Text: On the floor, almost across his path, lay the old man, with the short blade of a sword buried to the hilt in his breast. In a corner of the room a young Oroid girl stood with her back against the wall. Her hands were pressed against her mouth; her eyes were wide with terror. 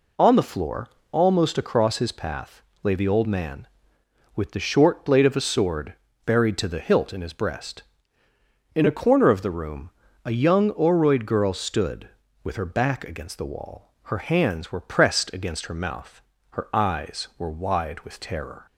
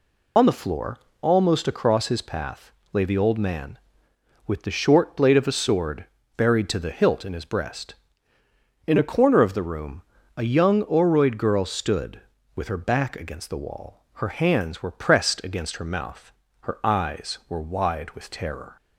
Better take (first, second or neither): first